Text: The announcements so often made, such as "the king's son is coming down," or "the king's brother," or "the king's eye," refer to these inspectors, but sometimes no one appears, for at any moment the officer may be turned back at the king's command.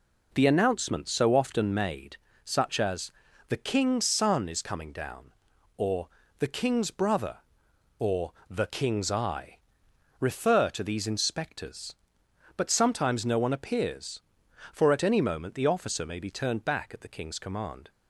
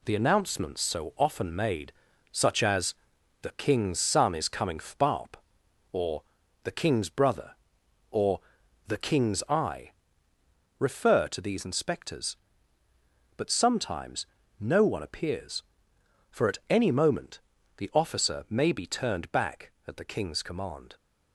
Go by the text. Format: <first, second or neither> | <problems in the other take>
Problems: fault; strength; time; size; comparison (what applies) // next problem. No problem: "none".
first | pauses between "as" and "the"; noticeable; at 2.9 s; 0.48 s long; also in the first // says "fbarp" for "down"; at 4.7 s // pauses between "or" and "the"; at 6.2 s; 0.40 s long; slight in the first // pauses between "or" and "the"; noticeable; at 8.3 s; 0.48 s long; slight in the first // pauses between "sometimes" and "no"; slight; at 14.2 s; 0.34 s long // pauses between "moment" and "the"; slight; at 17.4 s; 0.36 s long